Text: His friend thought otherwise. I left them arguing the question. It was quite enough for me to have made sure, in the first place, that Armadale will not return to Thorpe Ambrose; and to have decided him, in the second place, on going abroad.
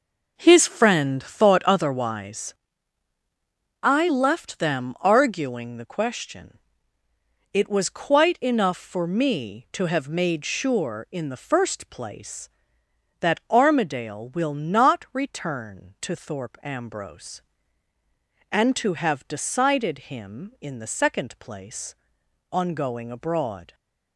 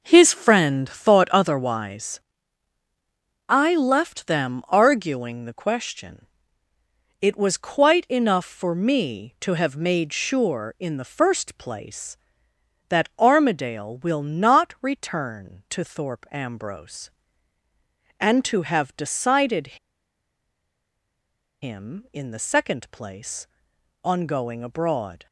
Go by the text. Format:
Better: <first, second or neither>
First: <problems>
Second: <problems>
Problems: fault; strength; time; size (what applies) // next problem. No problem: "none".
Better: first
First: none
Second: pauses between "decided" and "him"; strong; at 19.7 s; 1.8 s long